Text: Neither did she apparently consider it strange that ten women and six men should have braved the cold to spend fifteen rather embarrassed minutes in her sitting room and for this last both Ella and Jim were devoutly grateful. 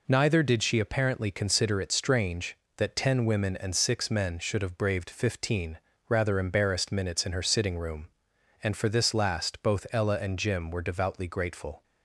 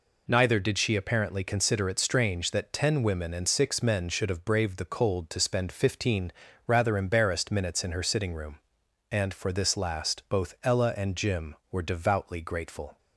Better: second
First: skips "the cold to spend"; at 5.0 s // pauses between "fifteen" and "rather"; slight; at 5.7 s; 0.30 s long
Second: pauses between "fifteen" and "rather"; slight; at 6.3 s; 0.34 s long

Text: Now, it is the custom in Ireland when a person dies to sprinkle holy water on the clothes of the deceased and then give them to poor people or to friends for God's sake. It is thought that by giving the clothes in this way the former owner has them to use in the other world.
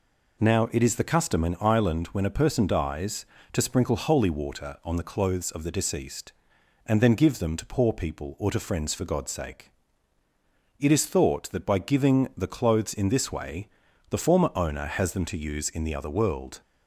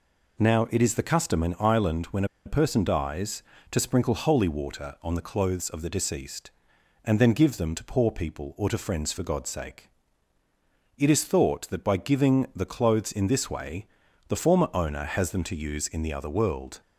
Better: first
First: pauses between "way" and "the"; at 13.6 s; 0.40 s long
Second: pauses between "when" and "a"; slight; at 2.2 s; 0.20 s long // pauses between "way" and "the"; at 13.8 s; 0.40 s long

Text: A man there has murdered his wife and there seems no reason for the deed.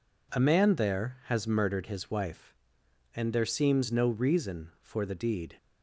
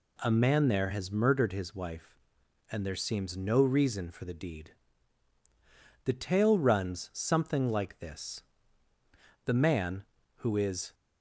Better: first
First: none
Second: goes on to say "The tale runs something like this The man who is"; strong; from 6.0 s on; 4.8 s long

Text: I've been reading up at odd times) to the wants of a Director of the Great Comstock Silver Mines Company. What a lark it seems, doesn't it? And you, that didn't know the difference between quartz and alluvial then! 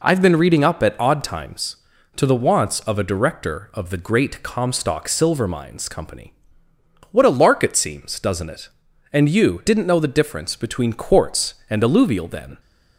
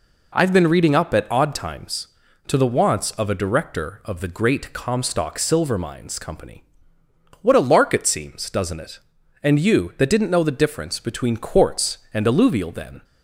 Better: second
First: skips "that"; at 9.6 s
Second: none

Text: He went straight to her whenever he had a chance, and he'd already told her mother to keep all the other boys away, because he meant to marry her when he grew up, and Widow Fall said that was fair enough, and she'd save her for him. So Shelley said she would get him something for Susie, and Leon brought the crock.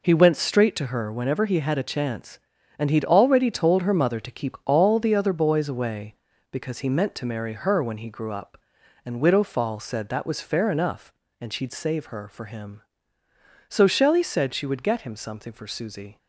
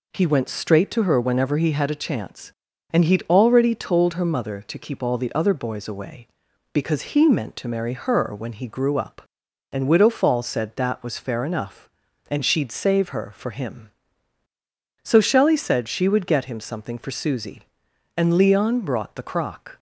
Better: second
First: stops before "and Leon brought the crock"; at 16.1 s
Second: none

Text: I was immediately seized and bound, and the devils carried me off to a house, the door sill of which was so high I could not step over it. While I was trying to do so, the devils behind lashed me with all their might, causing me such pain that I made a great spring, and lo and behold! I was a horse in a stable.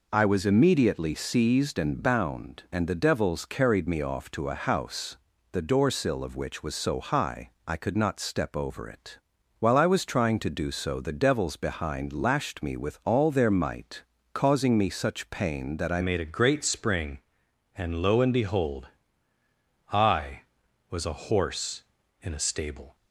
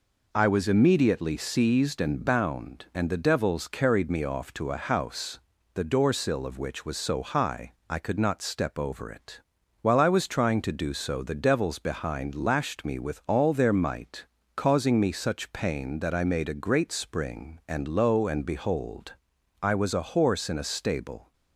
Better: second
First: pauses between "high" and "I"; slight; at 7.5 s; 0.16 s long // changes voice at "made"; from 16.0 s on; 6.9 s long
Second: pauses between "high" and "I"; slight; at 7.7 s; 0.16 s long

